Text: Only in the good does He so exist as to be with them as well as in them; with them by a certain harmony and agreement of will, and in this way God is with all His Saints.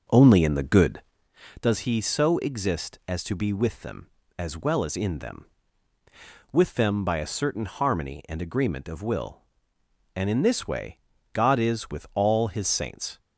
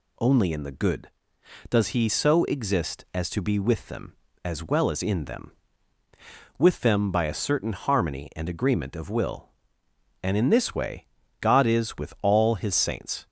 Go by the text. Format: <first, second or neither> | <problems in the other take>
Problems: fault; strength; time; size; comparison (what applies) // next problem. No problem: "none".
second | starts louder than the rest; until 1.4 s; 6.5 dB // pauses between "way" and "God"; slight; at 10.9 s; 0.34 s long; slight in the second